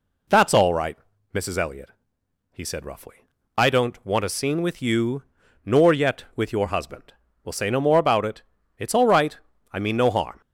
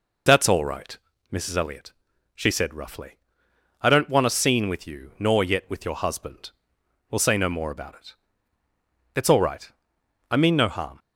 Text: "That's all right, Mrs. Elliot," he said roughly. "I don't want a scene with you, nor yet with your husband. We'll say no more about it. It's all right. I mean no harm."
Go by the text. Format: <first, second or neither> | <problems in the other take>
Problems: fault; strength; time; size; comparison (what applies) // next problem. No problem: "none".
first | says "she" for "he"; at 2.3 s